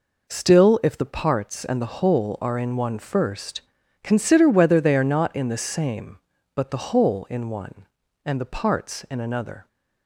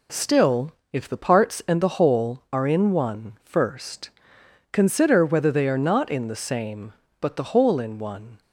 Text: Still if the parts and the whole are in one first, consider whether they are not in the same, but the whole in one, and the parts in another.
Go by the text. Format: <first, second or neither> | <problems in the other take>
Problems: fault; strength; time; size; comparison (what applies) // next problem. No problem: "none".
first | pauses between "Still" and "if"; slight; at 0.7 s; 0.18 s long // stops before "and the parts in another"; at 8.4 s